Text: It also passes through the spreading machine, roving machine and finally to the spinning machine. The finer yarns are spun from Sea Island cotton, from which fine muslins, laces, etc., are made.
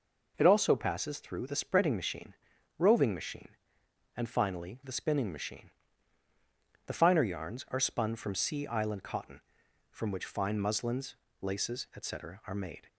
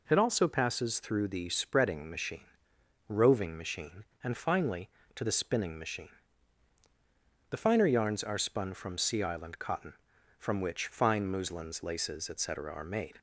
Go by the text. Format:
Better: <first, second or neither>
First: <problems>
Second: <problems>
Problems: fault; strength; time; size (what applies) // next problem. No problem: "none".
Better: second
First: skips "to"; at 4.8 s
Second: none